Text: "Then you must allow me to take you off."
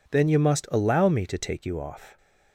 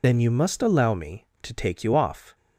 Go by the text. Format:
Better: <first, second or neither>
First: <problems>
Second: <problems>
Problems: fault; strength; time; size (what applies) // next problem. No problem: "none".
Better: first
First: none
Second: loses the start of "Then"; at 0.0 s; 70 ms